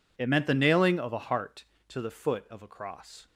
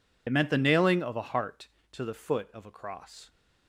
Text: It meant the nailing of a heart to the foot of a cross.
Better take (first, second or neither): first